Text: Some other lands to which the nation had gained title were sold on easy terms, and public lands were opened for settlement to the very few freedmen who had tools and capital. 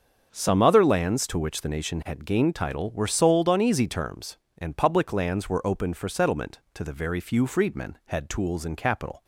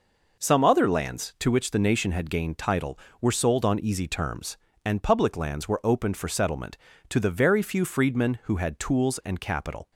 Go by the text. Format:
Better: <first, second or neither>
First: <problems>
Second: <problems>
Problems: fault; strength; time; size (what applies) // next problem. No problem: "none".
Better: second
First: starts louder than the rest; until 1.3 s; 7 dB // skips "who"; at 8.0 s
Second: none